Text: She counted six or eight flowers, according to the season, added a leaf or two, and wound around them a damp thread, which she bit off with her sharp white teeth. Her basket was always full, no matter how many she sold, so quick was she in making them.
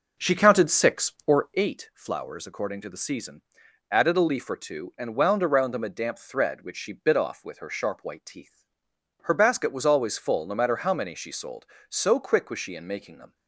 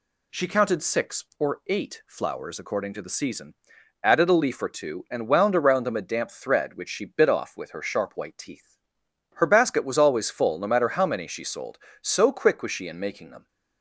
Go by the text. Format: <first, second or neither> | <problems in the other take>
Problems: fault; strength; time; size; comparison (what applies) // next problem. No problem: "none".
second | starts louder than the rest; noticeable; until 1.8 s; 5.5 dB